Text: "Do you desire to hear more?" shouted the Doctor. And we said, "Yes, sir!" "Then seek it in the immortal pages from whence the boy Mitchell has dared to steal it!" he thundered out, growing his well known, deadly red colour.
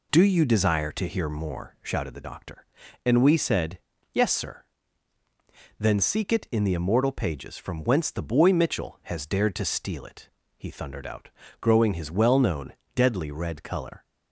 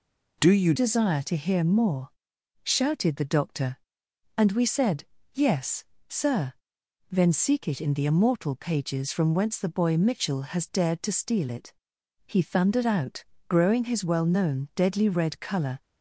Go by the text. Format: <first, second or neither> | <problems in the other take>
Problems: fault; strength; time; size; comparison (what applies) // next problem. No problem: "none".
first | changes voice at "desire"; from 0.7 s on; 15.1 s long